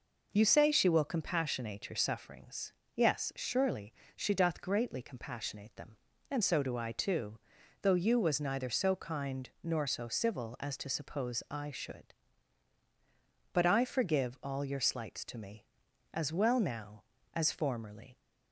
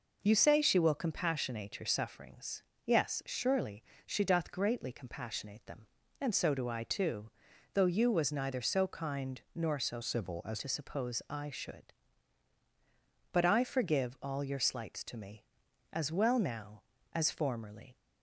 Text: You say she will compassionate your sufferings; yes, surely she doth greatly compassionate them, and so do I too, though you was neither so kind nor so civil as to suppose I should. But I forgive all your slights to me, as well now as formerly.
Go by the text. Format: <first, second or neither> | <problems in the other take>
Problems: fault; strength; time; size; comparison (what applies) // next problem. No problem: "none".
first | pauses between "surely" and "she"; slight; at 3.8 s; 0.24 s long; slight in the first // pauses between "kind" and "nor"; slight; at 9.3 s; 0.16 s long; slight in the first // changes voice from "civil" to "as"; from 10.0 to 10.6 s; 0.6 s long